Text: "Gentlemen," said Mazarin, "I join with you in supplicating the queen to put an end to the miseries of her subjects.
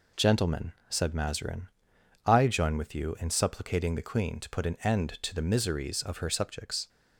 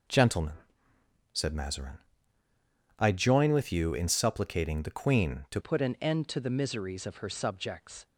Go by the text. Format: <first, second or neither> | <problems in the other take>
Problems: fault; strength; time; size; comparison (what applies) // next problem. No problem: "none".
first | changes voice at "put"; from 5.6 s on; 2.4 s long